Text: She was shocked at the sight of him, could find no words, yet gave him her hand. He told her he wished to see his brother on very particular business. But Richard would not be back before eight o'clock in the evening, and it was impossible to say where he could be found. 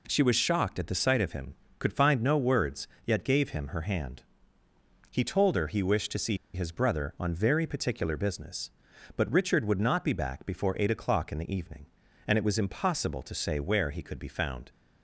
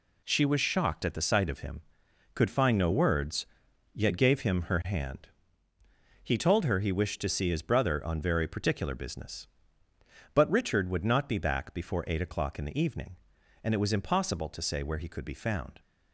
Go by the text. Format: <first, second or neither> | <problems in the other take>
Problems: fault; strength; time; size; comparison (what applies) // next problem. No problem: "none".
second | pauses between "see" and "his"; slight; at 6.3 s; 0.17 s long